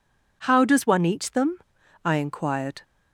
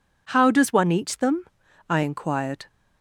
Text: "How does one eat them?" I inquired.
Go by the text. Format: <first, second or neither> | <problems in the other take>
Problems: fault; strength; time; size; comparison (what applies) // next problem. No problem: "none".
neither | none